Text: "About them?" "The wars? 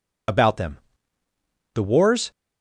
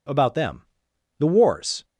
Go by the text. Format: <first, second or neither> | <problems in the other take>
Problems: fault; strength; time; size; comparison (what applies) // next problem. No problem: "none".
second | loses the start of "About"; at 0.2 s; 45 ms